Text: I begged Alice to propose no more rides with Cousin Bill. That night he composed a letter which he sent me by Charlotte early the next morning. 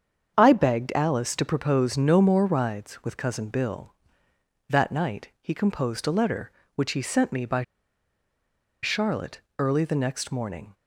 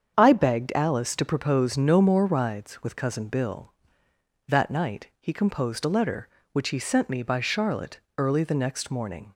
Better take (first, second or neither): second